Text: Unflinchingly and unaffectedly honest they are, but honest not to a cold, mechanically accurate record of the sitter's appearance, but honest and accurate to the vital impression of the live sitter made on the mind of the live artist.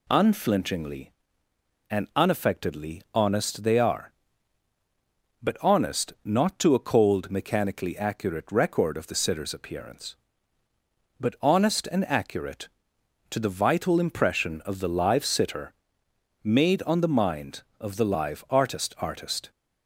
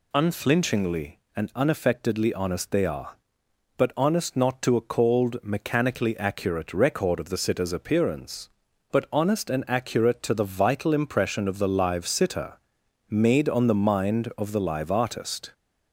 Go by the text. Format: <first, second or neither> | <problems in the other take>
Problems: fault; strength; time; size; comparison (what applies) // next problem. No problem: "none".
second | pauses between "sitter" and "made"; noticeable; at 15.7 s; 0.72 s long; noticeable in the second // says "artist" twice; at 18.9 s